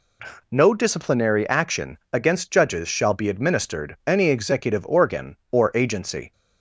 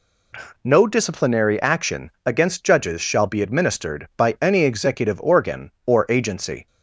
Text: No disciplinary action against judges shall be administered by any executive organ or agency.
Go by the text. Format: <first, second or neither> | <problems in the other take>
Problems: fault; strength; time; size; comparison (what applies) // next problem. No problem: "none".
second | pauses between "action" and "against"; slight; at 1.9 s; 0.16 s long; slight in the second // skips "by"; at 4.0 s